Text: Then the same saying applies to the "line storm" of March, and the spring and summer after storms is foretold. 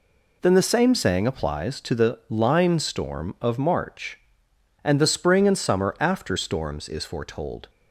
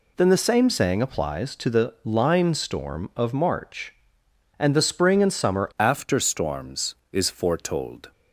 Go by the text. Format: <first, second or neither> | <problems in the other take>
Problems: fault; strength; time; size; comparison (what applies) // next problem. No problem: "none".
first | changes voice at "after"; from 5.7 s on; 2.4 s long